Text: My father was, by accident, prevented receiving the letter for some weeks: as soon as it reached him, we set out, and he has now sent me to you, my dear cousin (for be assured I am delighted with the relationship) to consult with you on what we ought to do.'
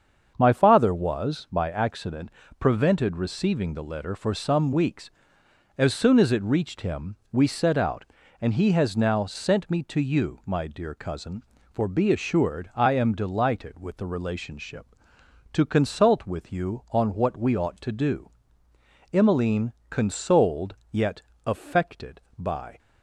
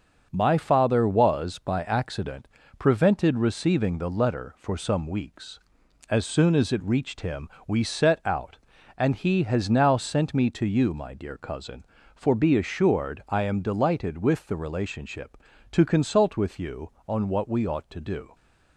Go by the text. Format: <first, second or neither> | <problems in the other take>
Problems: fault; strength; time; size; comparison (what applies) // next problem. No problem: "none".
second | starts louder than the rest; strong; until 1.3 s; 7 dB; also in the second // goes on to say "Emmeline consoled yet affected by"; strong; from 19.1 s on; 3.6 s long